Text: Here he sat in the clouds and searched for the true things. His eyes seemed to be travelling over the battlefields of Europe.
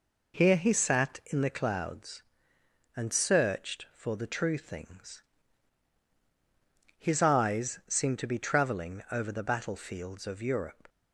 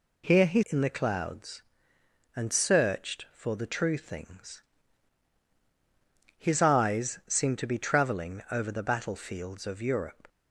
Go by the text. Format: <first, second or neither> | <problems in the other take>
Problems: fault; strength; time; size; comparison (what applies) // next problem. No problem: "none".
first | skips "sat"; at 0.6 s